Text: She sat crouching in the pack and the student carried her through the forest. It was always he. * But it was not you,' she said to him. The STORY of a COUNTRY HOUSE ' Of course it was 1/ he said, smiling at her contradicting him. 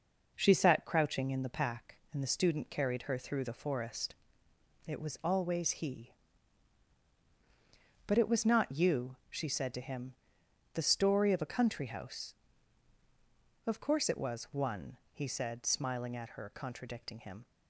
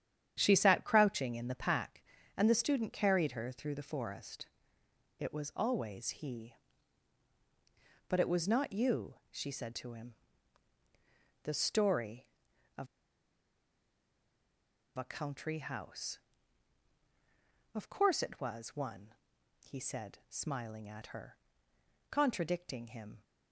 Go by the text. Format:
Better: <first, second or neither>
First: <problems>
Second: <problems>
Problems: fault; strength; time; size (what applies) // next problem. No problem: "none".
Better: first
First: none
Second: starts louder than the rest; strong; until 1.3 s; 9.5 dB // pauses between "of" and "a"; strong; at 12.8 s; 2.1 s long // pauses between "her" and "contradicting"; noticeable; at 21.3 s; 0.76 s long